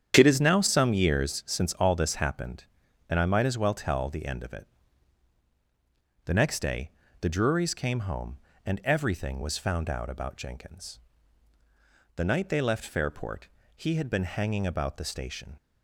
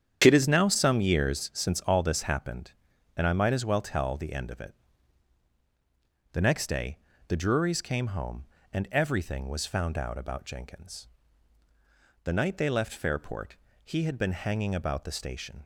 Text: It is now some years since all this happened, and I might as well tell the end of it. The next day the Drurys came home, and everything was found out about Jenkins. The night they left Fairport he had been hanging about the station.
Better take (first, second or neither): neither